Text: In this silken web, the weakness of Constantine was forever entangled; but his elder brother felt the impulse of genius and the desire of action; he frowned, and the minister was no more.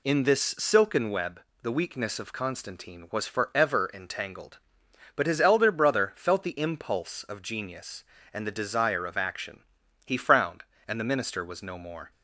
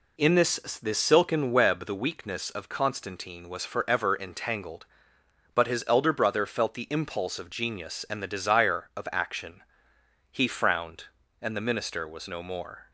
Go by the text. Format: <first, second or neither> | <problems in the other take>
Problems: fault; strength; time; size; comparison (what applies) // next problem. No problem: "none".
first | says "this" twice; at 0.8 s